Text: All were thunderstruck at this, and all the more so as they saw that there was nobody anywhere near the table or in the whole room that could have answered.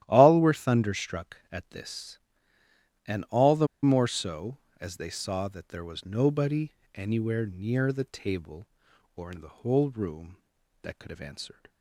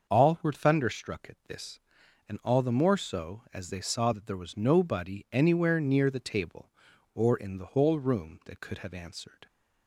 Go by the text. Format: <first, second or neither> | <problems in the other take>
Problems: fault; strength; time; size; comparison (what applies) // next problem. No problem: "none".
second | starts louder than the rest; strong; until 1.0 s; 12.5 dB; also in the second // pauses between "the" and "more"; slight; at 3.6 s; 0.17 s long // pauses between "nobody" and "anywhere"; slight; at 6.7 s; 0.24 s long